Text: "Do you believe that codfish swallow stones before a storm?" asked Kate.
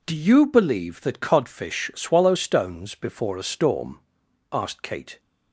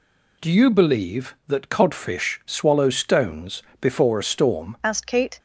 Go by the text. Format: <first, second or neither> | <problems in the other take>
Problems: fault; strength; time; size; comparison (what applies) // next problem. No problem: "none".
first | pauses between "stones" and "before"; slight; at 3.6 s; 0.20 s long // changes voice at "asked"; from 4.8 s on; 0.5 s long